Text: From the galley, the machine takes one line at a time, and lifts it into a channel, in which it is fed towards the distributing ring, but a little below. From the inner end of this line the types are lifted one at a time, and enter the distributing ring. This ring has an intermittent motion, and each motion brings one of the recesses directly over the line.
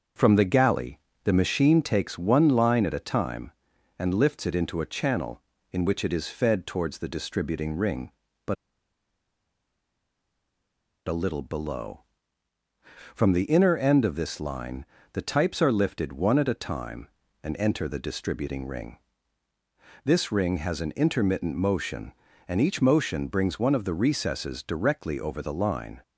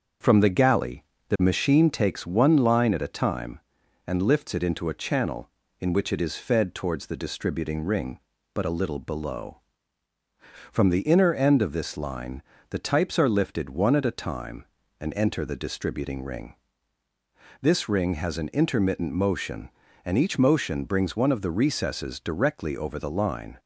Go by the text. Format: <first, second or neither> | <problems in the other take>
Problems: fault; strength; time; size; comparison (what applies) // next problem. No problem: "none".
second | starts louder than the rest; until 1.4 s; 7 dB; also in the second // pauses between "but" and "a"; strong; at 8.5 s; 2.5 s long // pauses between "line" and "the"; slight; at 14.8 s; 0.30 s long; slight in the second